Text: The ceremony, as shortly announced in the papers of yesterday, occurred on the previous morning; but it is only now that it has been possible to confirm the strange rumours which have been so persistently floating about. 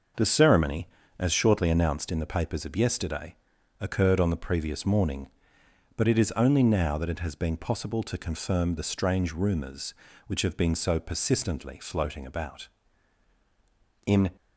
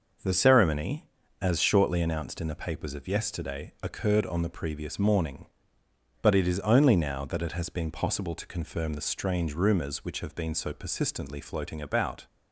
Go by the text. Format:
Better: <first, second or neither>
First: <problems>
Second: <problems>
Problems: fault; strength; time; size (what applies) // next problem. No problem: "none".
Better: second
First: starts louder than the rest; until 1.4 s; 6.5 dB // goes on to say "In"; slight; from 14.0 s on; 0.26 s long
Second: starts louder than the rest; noticeable; until 1.5 s; 6 dB